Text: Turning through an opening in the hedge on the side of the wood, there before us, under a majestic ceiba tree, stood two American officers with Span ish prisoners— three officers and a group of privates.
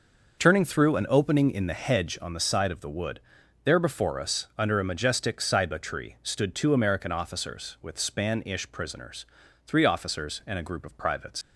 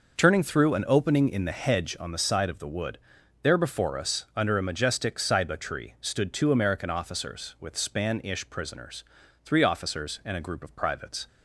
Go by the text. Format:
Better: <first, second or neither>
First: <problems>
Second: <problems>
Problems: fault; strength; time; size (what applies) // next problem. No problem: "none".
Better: second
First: leaves "privates" unfinished; at 11.4 s; 75 ms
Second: none